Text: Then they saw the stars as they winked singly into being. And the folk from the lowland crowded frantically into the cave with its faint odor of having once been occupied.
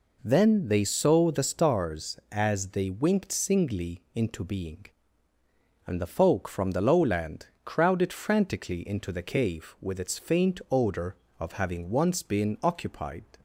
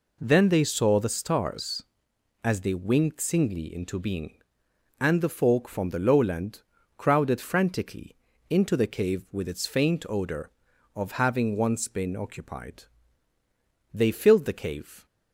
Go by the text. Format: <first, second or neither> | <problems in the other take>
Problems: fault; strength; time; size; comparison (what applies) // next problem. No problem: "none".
first | pauses between "lowland" and "crowded"; slight; at 6.6 s; 0.36 s long; slight in the first // pauses between "frantically" and "into"; slight; at 8.1 s; 0.34 s long // goes on to say "They filled the cave"; noticeable; from 13.9 s on; 1.1 s long